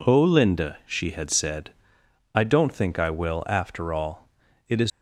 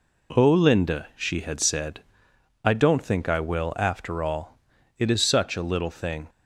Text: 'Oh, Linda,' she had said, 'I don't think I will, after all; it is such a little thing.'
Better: second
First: stops before "such a little thing"; at 4.9 s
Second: none

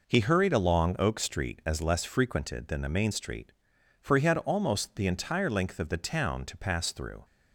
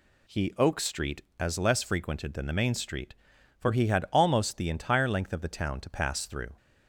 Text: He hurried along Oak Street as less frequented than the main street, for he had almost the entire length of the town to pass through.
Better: first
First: none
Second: skips "hurried along"; at 0.5 s

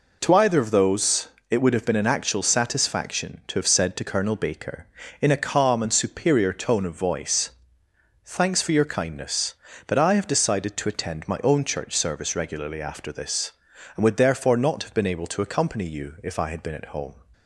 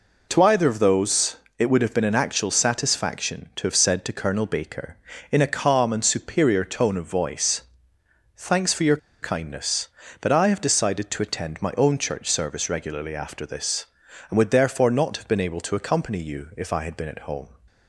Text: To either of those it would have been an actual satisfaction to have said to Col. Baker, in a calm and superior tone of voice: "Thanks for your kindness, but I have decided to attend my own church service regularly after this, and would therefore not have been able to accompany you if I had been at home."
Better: first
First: pauses between "those" and "it"; slight; at 1.2 s; 0.22 s long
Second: pauses between "those" and "it"; slight; at 1.3 s; 0.22 s long // pauses between "your" and "kindness"; slight; at 8.9 s; 0.24 s long

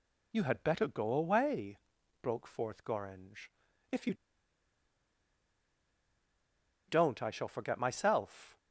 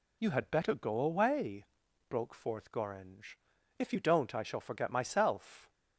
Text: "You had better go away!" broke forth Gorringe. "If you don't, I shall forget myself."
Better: second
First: pauses between "you" and "don't"; strong; at 4.1 s; 2.7 s long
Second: none

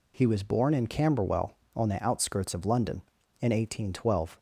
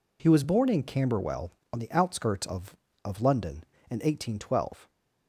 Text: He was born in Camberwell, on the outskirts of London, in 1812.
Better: first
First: none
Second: says "of" twice; at 3.0 s

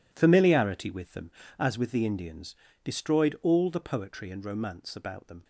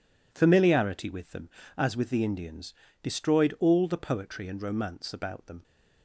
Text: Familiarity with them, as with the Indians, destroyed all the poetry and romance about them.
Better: second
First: gets quieter; strong; throughout; 12.5 dB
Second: none

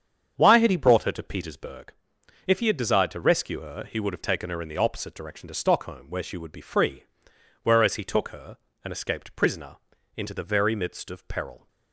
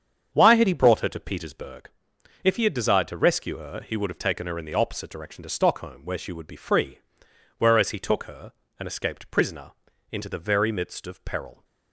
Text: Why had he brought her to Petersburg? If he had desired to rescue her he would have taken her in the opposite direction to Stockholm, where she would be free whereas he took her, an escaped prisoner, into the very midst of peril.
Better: neither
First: starts louder than the rest; strong; until 1.3 s; 7.5 dB // pauses between "free" and "whereas"; noticeable; at 7.0 s; 0.60 s long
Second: starts louder than the rest; strong; until 1.3 s; 7.5 dB // pauses between "free" and "whereas"; noticeable; at 6.9 s; 0.60 s long

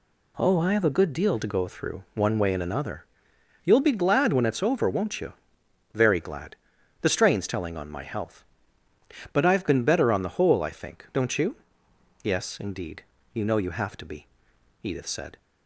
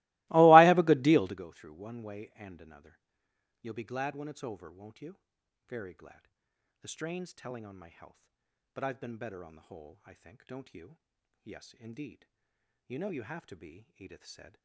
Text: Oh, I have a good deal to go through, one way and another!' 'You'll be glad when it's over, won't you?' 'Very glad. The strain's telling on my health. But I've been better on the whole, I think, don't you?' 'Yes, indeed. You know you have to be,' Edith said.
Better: first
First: none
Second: starts louder than the rest; strong; until 1.5 s; 22.5 dB

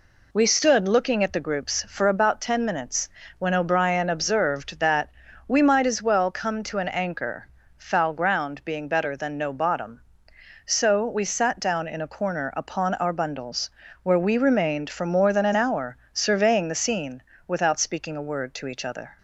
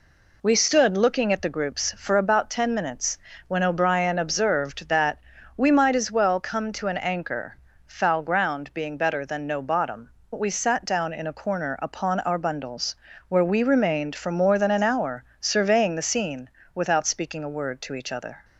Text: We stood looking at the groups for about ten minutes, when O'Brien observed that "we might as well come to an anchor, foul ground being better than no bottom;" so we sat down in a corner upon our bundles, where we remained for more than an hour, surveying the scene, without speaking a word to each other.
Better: first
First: pauses between "that" and "we"; at 5.0 s; 0.40 s long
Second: pauses between "that" and "we"; at 5.1 s; 0.40 s long // skips "so"; at 10.2 s

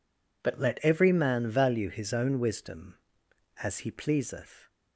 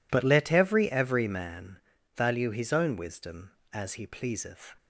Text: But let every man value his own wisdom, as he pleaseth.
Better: first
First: none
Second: says "every" twice; at 0.9 s // pauses between "man" and "value"; at 1.7 s; 0.38 s long

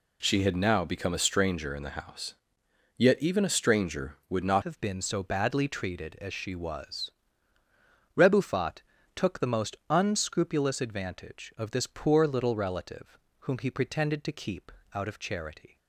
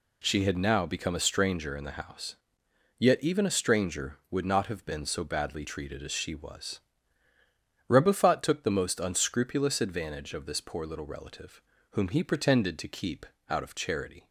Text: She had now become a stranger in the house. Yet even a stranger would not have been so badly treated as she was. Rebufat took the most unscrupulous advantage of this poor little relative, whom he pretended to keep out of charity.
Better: second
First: changes voice at "have"; from 4.6 s on; 11.1 s long // pauses between "Rebufat" and "took"; slight; at 8.8 s; 0.34 s long // pauses between "keep" and "out"; slight; at 14.7 s; 0.24 s long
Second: pauses between "keep" and "out"; slight; at 13.2 s; 0.24 s long

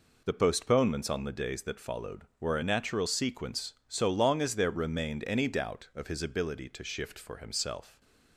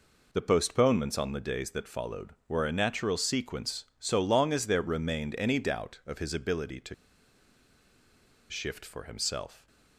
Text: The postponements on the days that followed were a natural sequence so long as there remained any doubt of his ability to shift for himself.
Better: first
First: none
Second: pauses between "to" and "shift"; strong; at 6.9 s; 1.5 s long

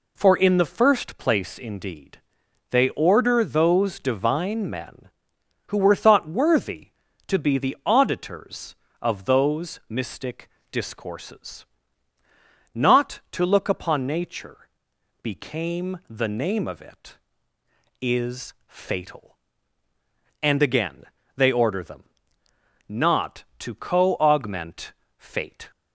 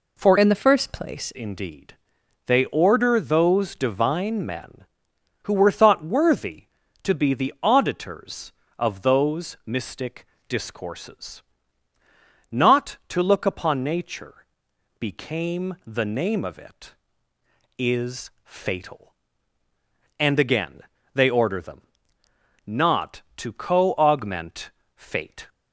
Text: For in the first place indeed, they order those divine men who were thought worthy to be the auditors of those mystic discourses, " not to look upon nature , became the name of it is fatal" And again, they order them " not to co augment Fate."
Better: first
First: pauses between "mystic" and "discourses"; slight; at 10.4 s; 0.24 s long // pauses between "augment" and "Fate"; slight; at 24.9 s; 0.26 s long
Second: changes voice from "in" to "place"; from 0.3 to 1.3 s; 1.0 s long // pauses between "mystic" and "discourses"; slight; at 10.2 s; 0.24 s long // pauses between "augment" and "Fate"; slight; at 24.7 s; 0.26 s long

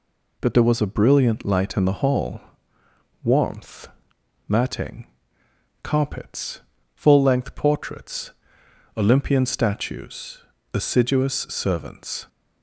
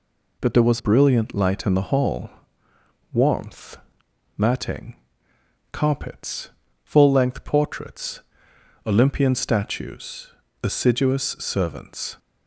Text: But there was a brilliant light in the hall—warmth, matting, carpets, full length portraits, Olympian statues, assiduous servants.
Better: first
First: none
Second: skips "a"; at 0.7 s

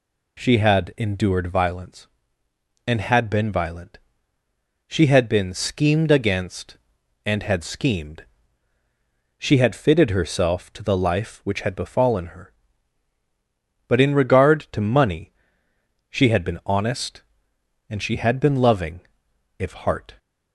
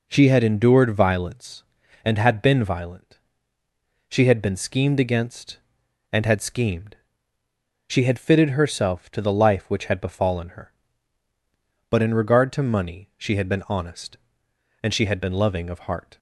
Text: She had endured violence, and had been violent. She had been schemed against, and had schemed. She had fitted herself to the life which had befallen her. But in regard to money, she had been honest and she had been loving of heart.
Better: second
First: says "if" for "of"; at 19.5 s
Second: none

